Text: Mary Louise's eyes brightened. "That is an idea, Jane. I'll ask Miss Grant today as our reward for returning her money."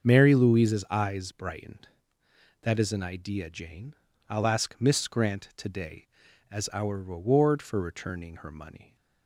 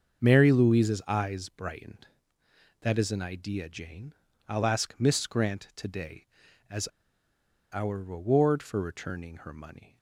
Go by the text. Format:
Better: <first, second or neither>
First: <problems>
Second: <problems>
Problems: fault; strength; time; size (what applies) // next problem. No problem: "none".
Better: first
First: starts louder than the rest; until 1.1 s; 6.5 dB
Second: starts louder than the rest; until 1.3 s; 6.5 dB // pauses between "as" and "our"; noticeable; at 6.8 s; 0.85 s long